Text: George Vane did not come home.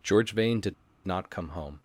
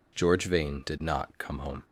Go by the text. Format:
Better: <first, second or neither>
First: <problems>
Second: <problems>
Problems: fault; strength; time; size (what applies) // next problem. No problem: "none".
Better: second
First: pauses between "did" and "not"; slight; at 0.7 s; 0.31 s long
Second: none